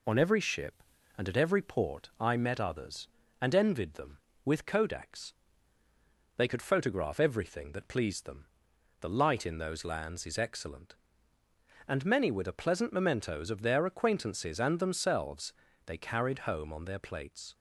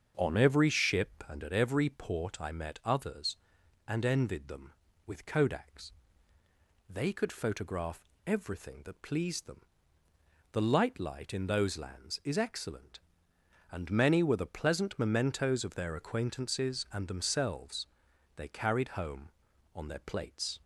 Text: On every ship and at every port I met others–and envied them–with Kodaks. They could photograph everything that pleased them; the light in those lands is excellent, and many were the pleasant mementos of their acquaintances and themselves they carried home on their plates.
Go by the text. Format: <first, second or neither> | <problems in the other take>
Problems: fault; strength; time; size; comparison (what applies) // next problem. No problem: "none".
first | starts louder than the rest; until 1.1 s; 7 dB // pauses between "photograph" and "everything"; slight; at 8.0 s; 0.18 s long // says "light" twice; at 10.9 s // pauses between "themselves" and "they"; noticeable; at 17.8 s; 0.48 s long; slight in the first